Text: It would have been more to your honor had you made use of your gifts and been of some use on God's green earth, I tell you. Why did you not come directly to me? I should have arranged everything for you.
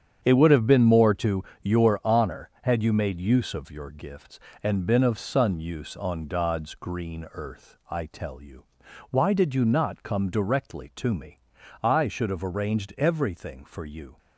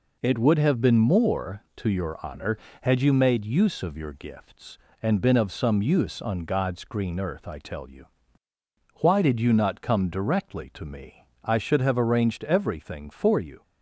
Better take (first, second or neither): second